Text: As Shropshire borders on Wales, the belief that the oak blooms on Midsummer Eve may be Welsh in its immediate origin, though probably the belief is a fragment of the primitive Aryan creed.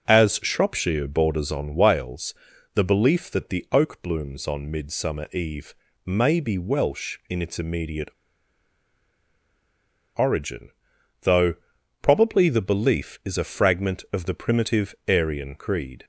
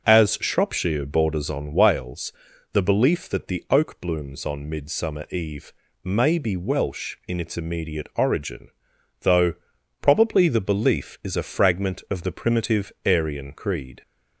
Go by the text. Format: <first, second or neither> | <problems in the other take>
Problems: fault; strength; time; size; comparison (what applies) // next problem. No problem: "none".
second | pauses between "Eve" and "may"; slight; at 5.7 s; 0.32 s long; slight in the second // pauses between "immediate" and "origin"; strong; at 8.1 s; 2.0 s long // pauses between "though" and "probably"; noticeable; at 11.5 s; 0.48 s long; noticeable in the second